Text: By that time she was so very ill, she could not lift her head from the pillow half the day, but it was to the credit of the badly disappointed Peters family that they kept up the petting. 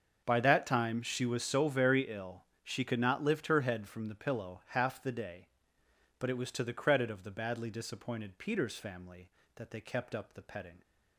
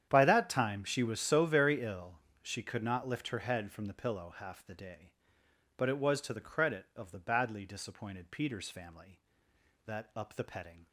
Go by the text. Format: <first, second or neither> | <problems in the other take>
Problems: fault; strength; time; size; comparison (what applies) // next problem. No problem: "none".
first | starts louder than the rest; strong; until 1.1 s; 9 dB; also in the first // skips "they kept"; at 10.1 s